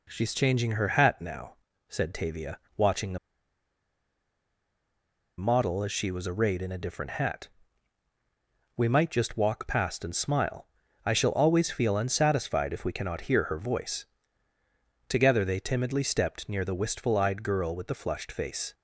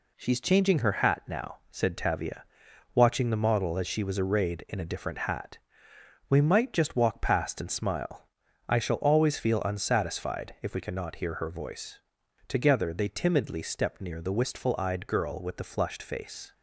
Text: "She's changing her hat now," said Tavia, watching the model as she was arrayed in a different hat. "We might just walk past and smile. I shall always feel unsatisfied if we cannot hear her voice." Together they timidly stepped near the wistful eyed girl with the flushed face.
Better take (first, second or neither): second